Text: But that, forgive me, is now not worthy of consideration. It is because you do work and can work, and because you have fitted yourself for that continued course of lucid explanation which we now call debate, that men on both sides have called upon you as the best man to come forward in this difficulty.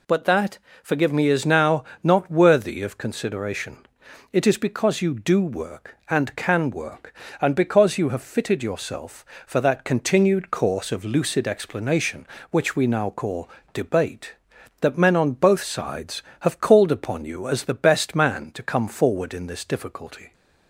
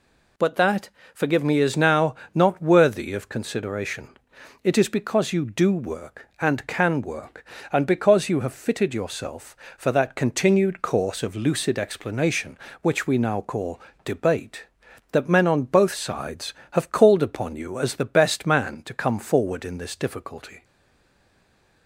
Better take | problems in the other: first | pauses between "now" and "not"; slight; at 2.1 s; 0.18 s long; slight in the first // pauses between "call" and "debate"; slight; at 13.7 s; 0.24 s long; slight in the first // stays silent after the last word; noticeable; from 20.6 s on; 1.2 s long

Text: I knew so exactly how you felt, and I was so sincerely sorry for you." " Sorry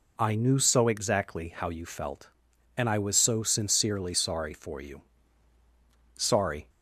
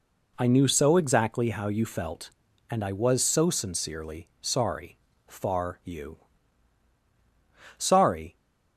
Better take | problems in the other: first | says "far" for "for"; at 5.2 s

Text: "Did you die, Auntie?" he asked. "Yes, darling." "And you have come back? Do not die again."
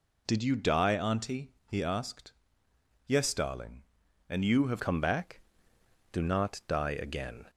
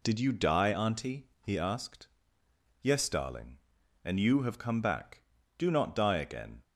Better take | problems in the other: second | changes voice at "come"; from 4.8 s on; 2.6 s long

